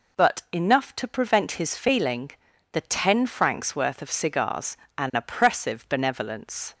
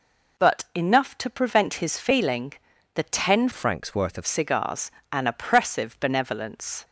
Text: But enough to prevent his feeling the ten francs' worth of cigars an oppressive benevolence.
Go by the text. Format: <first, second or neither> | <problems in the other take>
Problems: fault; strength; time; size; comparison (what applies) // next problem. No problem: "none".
first | pauses between "feeling" and "the"; at 2.5 s; 0.40 s long; also in the first // changes voice from "francs" to "of"; from 3.5 to 4.2 s; 0.7 s long // pauses between "cigars" and "an"; slight; at 4.9 s; 0.20 s long; slight in the first